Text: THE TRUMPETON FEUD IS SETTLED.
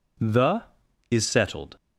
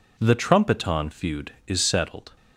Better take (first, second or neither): second